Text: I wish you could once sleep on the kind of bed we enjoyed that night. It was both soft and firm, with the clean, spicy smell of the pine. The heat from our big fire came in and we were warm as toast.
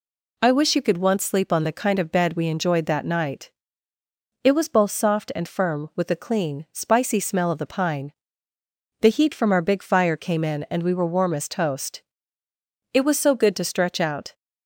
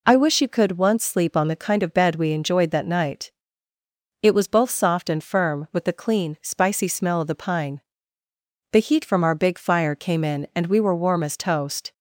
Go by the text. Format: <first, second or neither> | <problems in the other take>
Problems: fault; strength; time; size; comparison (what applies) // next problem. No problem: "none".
second | goes on to say "It was so good to stretch out"; from 12.9 s on; 1.4 s long